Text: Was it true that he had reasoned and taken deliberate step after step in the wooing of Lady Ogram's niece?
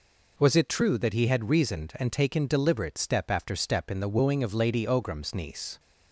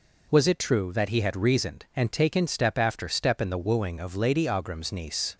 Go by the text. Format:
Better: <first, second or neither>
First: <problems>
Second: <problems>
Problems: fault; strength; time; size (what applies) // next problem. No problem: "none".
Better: first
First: none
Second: skips "deliberate"; at 2.4 s